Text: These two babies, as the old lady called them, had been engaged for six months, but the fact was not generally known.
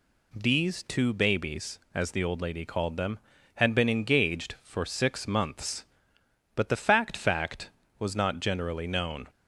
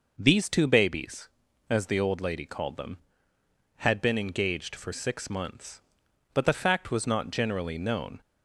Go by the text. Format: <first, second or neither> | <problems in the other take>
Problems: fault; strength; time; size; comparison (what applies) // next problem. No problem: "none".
second | says "fact" twice; at 7.1 s